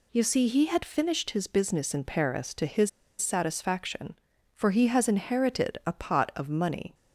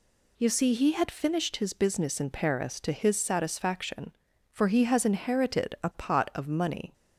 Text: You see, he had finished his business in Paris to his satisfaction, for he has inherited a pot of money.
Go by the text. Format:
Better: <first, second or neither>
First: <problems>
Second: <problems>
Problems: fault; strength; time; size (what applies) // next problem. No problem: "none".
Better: second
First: pauses between "his" and "satisfaction"; slight; at 2.8 s; 0.30 s long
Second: none